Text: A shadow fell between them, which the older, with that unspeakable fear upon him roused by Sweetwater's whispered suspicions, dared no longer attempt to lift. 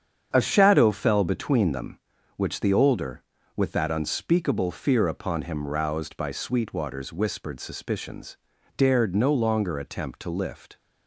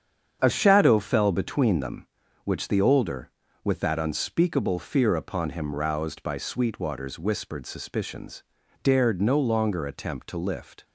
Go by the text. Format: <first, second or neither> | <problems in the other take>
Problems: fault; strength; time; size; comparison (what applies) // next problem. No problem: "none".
neither | starts louder than the rest; strong; the same in both